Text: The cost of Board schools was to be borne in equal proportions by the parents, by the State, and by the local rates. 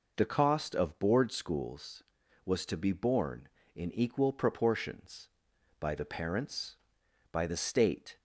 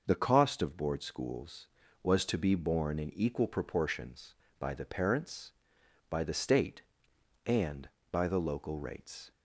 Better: second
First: stops before "and by the local rates"; at 8.1 s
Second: none

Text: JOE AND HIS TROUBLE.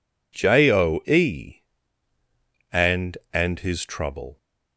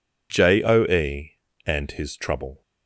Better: second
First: says "AND" twice; at 3.3 s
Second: none

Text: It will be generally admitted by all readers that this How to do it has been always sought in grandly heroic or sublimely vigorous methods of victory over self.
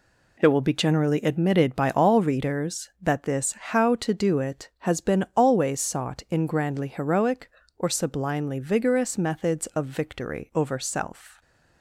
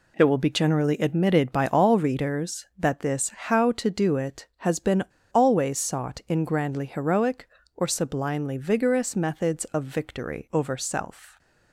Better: first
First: none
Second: pauses between "been" and "always"; slight; at 5.0 s; 0.29 s long

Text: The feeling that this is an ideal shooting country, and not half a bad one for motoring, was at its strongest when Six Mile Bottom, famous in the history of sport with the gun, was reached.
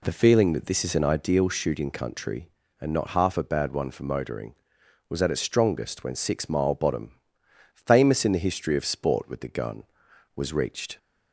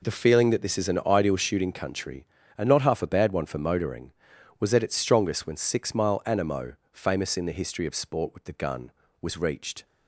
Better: first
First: none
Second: says "Animo" for "Bottom"; at 6.2 s

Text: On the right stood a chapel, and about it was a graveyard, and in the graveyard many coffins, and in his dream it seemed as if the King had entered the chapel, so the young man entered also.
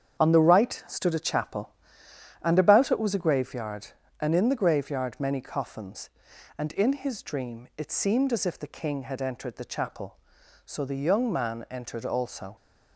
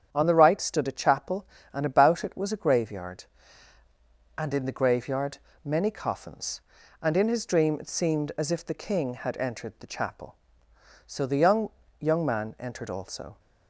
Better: first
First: starts louder than the rest; strong; until 1.2 s; 8 dB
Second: starts louder than the rest; strong; until 1.1 s; 8.5 dB // pauses between "graveyard" and "many"; slight; at 5.3 s; 0.26 s long // says "young" twice; at 12.0 s

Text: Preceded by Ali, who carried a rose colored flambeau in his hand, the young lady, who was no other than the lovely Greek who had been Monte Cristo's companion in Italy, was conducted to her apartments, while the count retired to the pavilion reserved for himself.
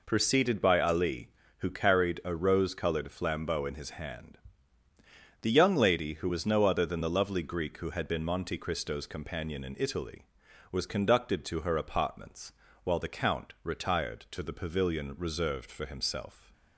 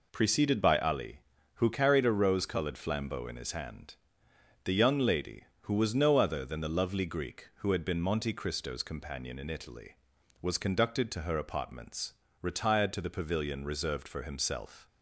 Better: first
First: none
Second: skips "while the count"; at 12.2 s

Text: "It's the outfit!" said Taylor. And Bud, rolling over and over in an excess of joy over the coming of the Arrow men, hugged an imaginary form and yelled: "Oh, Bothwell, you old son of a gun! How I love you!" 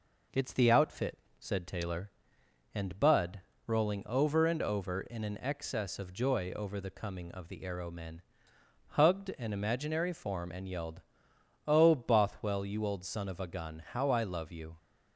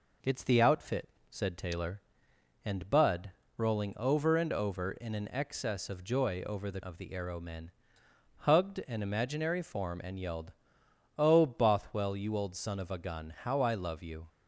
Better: first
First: none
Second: skips "coming"; at 6.8 s

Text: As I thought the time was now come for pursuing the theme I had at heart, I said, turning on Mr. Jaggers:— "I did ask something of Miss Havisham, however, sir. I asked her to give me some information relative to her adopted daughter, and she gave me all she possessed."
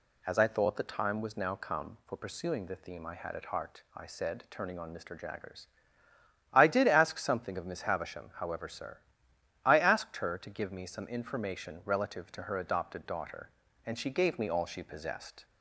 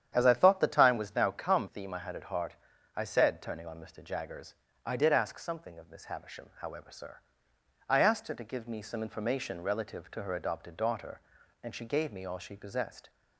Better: first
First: none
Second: starts louder than the rest; strong; until 1.1 s; 9.5 dB // skips "for pursuing the"; at 1.6 s

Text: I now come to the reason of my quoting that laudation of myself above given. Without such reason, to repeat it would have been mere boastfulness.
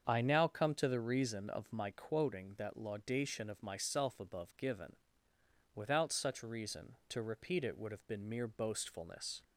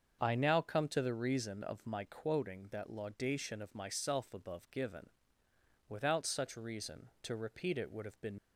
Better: first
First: starts louder than the rest; until 1.0 s; 7 dB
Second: starts louder than the rest; until 1.2 s; 6.5 dB // stops before "mere boastfulness"; at 8.3 s

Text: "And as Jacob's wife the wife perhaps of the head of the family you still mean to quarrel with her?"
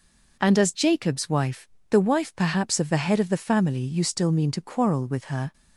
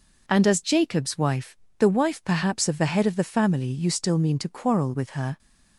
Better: neither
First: pauses between "wife" and "the"; slight; at 1.6 s; 0.22 s long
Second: pauses between "wife" and "the"; slight; at 1.5 s; 0.22 s long

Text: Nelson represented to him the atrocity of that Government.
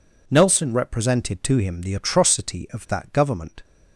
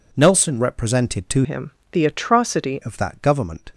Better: first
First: none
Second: changes voice from "him" to "atrocity"; from 1.4 to 2.8 s; 1.4 s long // pauses between "him" and "the"; slight; at 1.7 s; 0.20 s long

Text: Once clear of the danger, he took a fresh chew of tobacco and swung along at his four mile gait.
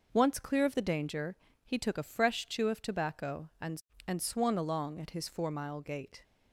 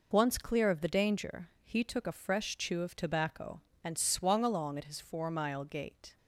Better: second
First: says "and" twice; at 4.0 s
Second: none

